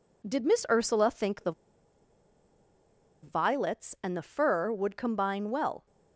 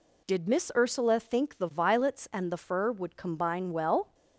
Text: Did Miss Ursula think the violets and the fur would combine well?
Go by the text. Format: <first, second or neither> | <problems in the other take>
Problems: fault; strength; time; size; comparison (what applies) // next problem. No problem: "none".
second | pauses between "the" and "violets"; strong; at 1.5 s; 1.7 s long